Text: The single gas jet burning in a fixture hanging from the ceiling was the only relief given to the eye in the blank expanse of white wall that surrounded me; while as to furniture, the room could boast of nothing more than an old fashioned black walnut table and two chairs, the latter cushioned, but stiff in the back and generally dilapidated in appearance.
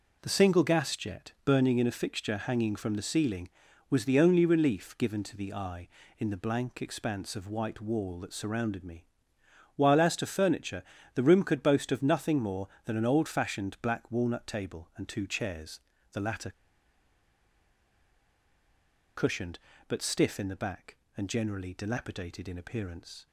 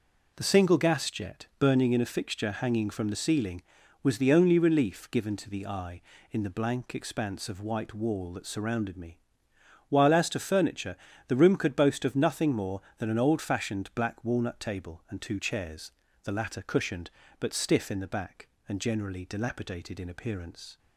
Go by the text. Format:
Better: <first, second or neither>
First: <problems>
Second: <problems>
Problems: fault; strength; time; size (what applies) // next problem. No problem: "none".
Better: second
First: pauses between "latter" and "cushioned"; strong; at 16.5 s; 2.6 s long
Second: none